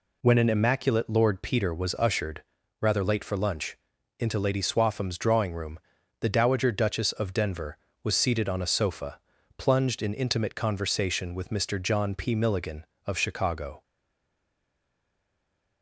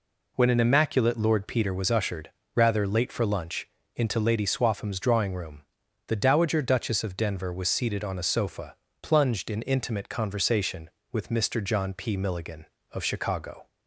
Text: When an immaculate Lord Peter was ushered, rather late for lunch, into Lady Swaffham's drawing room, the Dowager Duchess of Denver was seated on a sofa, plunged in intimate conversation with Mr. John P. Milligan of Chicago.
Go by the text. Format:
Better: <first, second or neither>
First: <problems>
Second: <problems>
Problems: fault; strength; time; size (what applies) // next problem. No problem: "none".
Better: second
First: stays silent after the last word; noticeable; from 13.8 s on; 2.0 s long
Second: none